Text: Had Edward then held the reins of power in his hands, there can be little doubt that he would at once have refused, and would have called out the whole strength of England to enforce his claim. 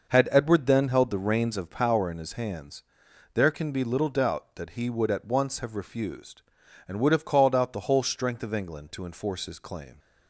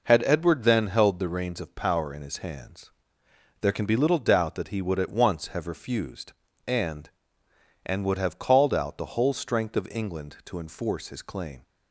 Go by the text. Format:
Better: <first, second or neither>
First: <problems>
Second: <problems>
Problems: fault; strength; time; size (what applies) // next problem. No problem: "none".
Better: first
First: none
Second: says "and" twice; at 7.8 s